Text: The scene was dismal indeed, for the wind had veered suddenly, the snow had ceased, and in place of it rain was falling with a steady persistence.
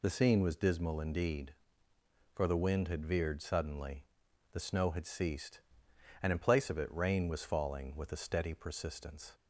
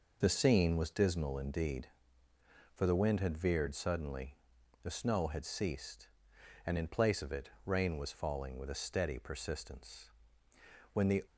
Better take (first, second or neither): first